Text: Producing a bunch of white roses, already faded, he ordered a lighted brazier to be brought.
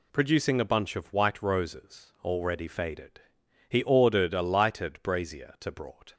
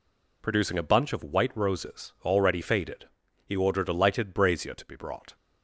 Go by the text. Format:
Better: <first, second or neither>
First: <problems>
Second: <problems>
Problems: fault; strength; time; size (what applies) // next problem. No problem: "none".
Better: second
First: skips "be"; at 5.6 s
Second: none